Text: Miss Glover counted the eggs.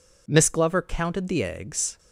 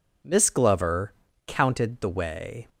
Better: first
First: none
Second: pauses between "Glover" and "counted"; slight; at 1.1 s; 0.34 s long // says "way" for "eggs"; at 2.1 s

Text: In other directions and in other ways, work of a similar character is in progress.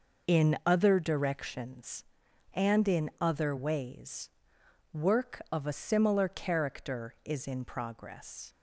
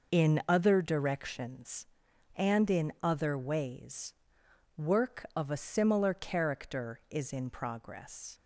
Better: neither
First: none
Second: none

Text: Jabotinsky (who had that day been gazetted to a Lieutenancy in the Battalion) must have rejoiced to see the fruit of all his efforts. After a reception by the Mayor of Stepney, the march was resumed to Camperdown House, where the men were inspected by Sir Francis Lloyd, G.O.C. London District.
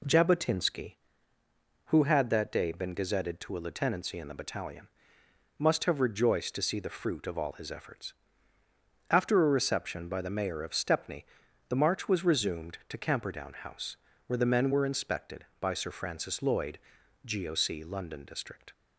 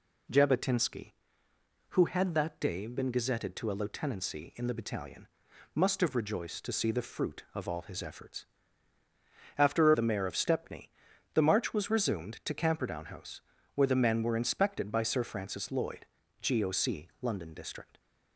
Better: first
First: none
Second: skips "a reception by"; at 9.9 s

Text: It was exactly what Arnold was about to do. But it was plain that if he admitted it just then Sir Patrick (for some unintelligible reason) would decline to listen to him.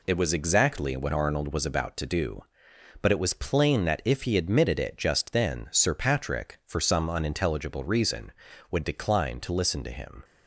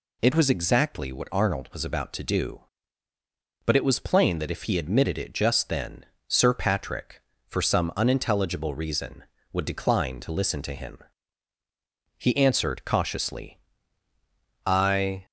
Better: first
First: none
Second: pauses between "then" and "Sir"; slight; at 6.0 s; 0.24 s long // goes on to say "He answered cautiously I"; strong; from 12.1 s on; 3.0 s long

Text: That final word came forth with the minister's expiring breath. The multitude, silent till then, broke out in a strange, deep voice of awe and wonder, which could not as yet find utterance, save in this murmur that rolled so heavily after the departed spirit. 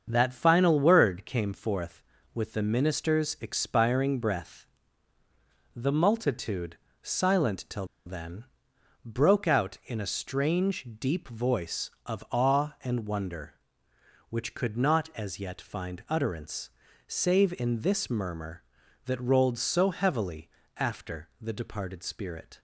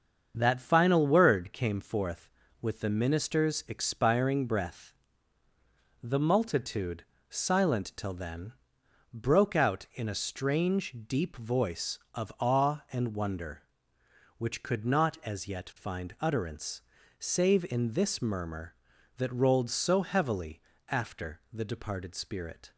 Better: second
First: starts louder than the rest; until 1.0 s; 7 dB // pauses between "till" and "then"; slight; at 7.8 s; 0.21 s long // pauses between "heavily" and "after"; slight; at 20.4 s; 0.28 s long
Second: starts louder than the rest; until 1.3 s; 7 dB // pauses between "heavily" and "after"; slight; at 20.6 s; 0.28 s long

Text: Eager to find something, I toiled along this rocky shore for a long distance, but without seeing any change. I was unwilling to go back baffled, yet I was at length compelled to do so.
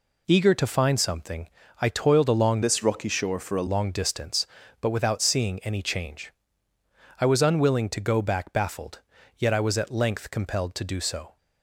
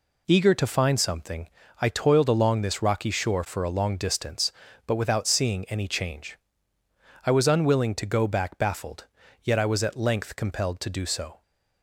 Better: second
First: changes voice from "this" to "a"; from 2.6 to 3.6 s; 1.0 s long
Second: none

